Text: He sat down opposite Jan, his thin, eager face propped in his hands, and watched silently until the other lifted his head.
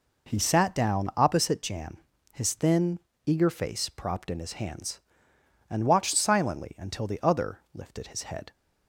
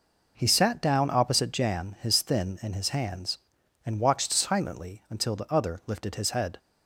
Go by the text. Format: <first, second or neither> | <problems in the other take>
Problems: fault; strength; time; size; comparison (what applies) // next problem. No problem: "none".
first | skips "eager face propped"; at 2.6 s